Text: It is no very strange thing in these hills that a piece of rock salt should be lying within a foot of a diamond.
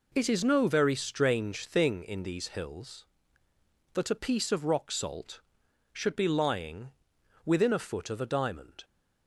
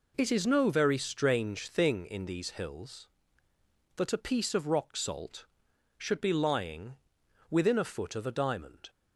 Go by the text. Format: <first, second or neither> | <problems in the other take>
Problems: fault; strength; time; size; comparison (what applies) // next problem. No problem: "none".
neither | pauses between "lying" and "within"; noticeable; the same in both